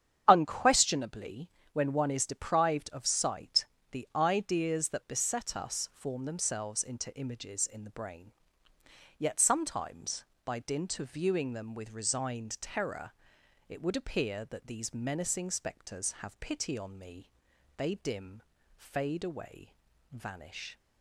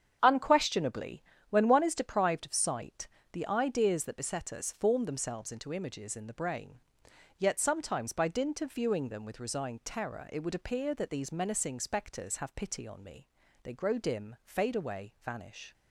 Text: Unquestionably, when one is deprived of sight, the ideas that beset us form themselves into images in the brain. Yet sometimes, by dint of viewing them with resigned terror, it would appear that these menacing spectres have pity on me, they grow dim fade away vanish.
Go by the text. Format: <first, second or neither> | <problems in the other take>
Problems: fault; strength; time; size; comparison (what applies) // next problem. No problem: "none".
second | starts louder than the rest; strong; until 1.2 s; 8.5 dB; strong in the second // skips "grow"; at 17.9 s // pauses between "dim" and "fade"; slight; at 18.4 s; 0.34 s long // pauses between "away" and "vanish"; at 19.7 s; 0.38 s long